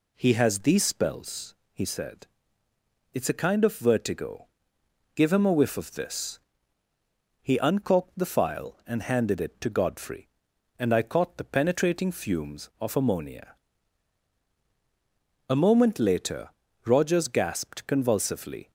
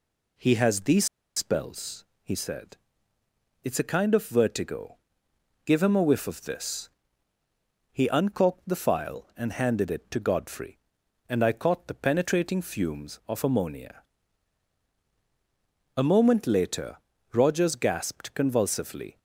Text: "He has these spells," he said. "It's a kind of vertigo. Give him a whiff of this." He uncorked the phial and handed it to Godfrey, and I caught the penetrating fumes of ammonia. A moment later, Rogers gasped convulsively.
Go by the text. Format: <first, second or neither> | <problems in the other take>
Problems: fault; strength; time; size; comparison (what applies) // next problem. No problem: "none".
first | pauses between "these" and "spells"; slight; at 1.0 s; 0.31 s long